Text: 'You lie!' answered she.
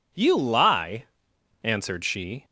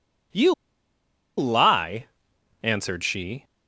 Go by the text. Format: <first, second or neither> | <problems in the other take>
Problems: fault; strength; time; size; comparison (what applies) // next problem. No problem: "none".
first | pauses between "You" and "lie"; noticeable; at 0.5 s; 0.83 s long